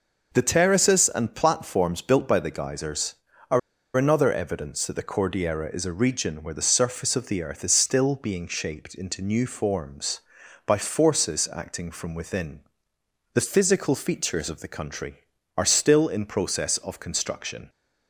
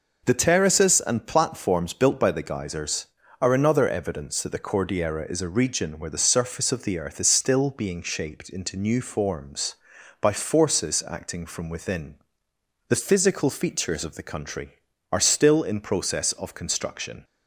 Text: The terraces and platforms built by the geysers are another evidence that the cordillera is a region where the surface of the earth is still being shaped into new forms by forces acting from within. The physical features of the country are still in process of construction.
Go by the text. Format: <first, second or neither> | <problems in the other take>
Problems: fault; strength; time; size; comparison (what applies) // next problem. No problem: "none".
second | pauses between "are" and "another"; at 3.5 s; 0.37 s long